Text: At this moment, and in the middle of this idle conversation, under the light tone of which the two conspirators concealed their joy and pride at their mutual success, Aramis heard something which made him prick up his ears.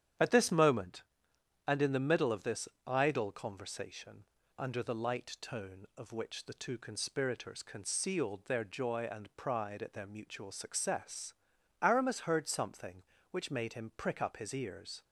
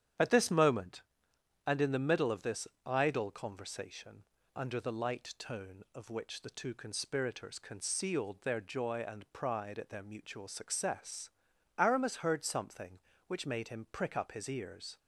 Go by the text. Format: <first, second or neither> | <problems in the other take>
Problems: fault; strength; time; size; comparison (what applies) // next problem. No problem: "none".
neither | starts louder than the rest; strong; the same in both // pauses between "this" and "idle"; slight; the same in both